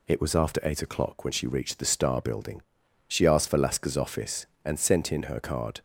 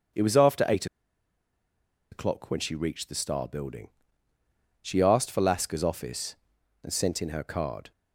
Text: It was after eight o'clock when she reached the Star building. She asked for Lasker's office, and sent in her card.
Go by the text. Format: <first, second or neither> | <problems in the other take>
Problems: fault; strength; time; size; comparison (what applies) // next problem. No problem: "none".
first | starts louder than the rest; until 2.4 s; 6 dB // pauses between "eight" and "o'clock"; strong; at 0.8 s; 1.2 s long